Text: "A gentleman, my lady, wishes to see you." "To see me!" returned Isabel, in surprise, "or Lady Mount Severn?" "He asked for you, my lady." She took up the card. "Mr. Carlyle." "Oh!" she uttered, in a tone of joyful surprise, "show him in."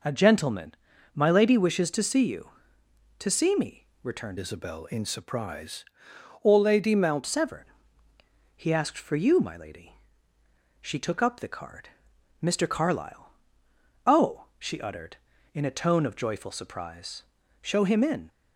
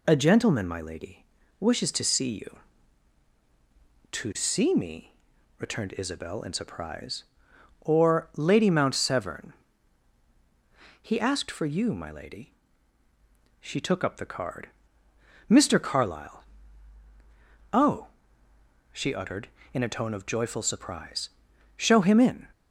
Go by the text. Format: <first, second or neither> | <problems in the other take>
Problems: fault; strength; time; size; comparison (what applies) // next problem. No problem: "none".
second | changes voice from "Isabel" to "Mount"; from 4.3 to 7.2 s; 2.9 s long